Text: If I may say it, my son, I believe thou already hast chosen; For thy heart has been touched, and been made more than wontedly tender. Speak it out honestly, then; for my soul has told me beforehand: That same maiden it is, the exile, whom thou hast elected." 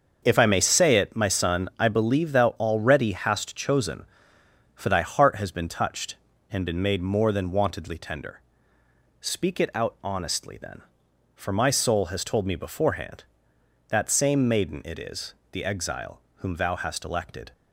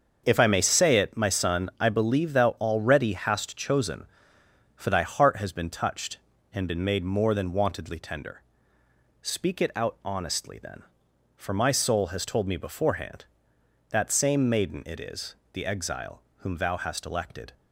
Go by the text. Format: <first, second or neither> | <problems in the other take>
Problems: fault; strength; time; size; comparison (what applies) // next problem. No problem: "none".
neither | starts louder than the rest; the same in both